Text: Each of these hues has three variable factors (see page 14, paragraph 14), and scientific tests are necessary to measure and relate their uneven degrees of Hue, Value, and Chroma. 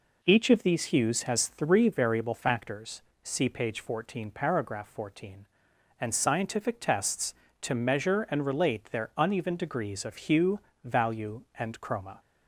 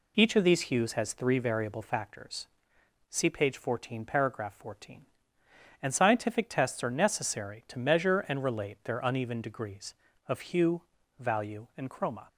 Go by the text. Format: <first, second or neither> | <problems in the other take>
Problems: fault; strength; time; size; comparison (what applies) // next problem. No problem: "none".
second | skips "are necessary"; at 7.4 s